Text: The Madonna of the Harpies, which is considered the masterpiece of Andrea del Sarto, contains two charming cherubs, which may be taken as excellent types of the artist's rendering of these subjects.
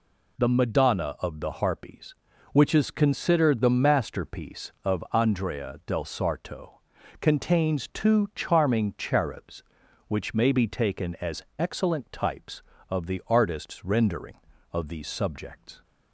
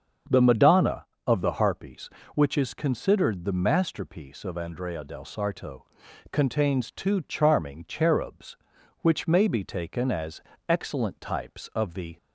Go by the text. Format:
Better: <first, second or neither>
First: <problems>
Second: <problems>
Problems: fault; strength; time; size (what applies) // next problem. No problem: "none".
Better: first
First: pauses between "as" and "excellent"; slight; at 11.4 s; 0.16 s long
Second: starts louder than the rest; until 1.4 s; 7 dB // pauses between "as" and "excellent"; at 10.4 s; 0.42 s long // stops before "artist's rendering of these subjects"; at 12.1 s